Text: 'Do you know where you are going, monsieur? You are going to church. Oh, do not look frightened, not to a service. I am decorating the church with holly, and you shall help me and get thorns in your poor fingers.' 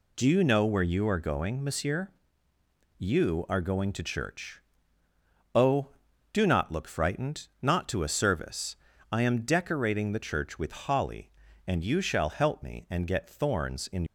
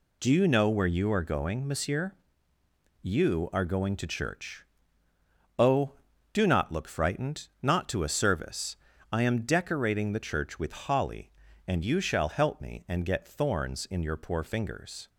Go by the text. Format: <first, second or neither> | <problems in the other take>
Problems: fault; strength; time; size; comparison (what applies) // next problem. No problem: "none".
second | stops before "your poor fingers"; at 14.0 s